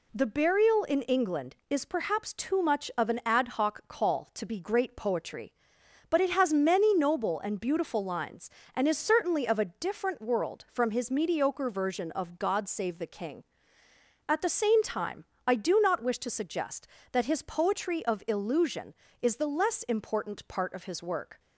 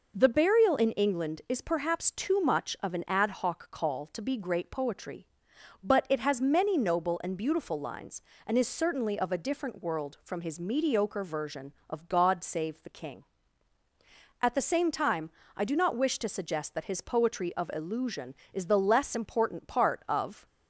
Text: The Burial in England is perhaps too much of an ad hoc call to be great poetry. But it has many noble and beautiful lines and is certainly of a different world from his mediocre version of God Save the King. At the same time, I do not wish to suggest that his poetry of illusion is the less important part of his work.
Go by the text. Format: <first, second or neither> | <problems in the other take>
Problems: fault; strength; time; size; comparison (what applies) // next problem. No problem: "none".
first | stops before "his work"; at 20.4 s